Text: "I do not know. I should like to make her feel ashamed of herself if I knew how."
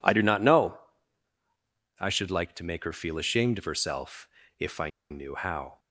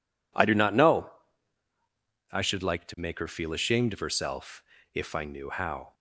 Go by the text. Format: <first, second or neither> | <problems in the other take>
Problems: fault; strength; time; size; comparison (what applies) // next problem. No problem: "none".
second | pauses between "herself" and "if"; slight; at 4.2 s; 0.32 s long; slight in the second // pauses between "I" and "knew"; slight; at 4.8 s; 0.22 s long